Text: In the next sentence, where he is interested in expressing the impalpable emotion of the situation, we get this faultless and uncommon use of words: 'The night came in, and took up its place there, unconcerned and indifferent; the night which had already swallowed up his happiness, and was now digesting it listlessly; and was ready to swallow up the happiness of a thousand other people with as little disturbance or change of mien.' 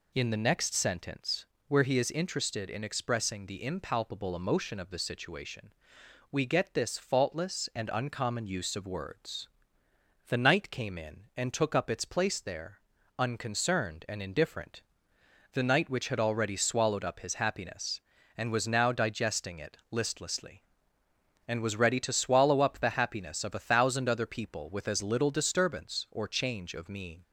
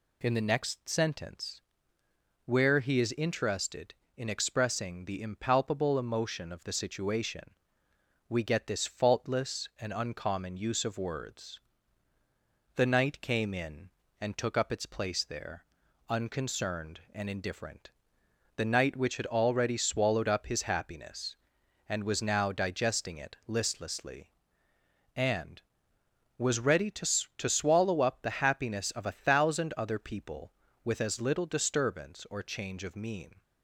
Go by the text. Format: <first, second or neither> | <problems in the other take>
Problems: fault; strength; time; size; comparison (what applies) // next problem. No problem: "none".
first | says "to" twice; at 27.3 s